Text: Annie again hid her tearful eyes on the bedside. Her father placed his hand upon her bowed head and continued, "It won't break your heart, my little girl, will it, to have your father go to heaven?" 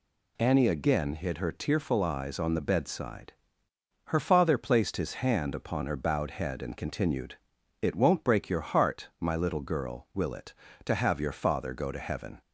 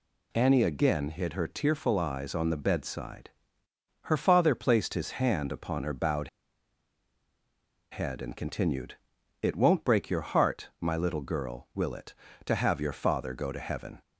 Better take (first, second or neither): first